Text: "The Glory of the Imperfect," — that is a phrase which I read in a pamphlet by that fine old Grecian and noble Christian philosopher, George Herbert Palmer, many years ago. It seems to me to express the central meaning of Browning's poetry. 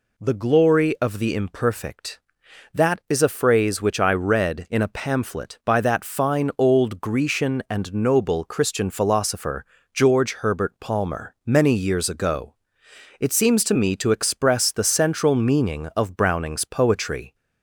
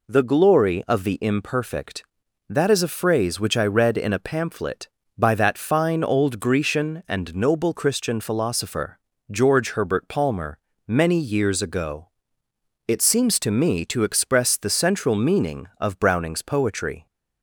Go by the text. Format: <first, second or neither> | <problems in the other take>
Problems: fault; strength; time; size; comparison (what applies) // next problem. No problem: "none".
neither | none